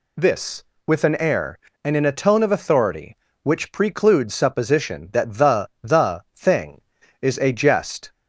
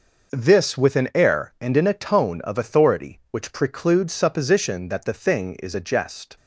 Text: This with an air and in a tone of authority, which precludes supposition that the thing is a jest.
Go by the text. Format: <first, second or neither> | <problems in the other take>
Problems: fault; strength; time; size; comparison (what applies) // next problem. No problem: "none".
second | says "the" twice; at 5.8 s